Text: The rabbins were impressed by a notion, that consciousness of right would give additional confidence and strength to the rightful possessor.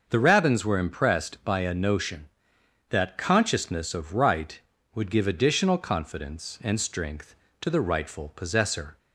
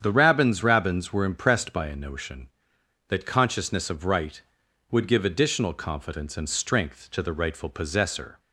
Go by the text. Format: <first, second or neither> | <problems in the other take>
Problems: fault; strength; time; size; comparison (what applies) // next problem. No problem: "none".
first | starts louder than the rest; strong; until 1.0 s; 8 dB; noticeable in the first // says "rabbins" twice; at 0.6 s